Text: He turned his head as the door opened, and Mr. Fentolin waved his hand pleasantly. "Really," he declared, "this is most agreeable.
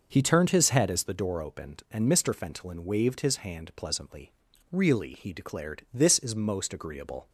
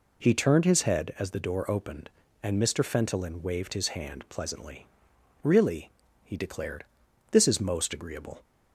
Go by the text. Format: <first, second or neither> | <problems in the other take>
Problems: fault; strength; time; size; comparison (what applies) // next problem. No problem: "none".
neither | none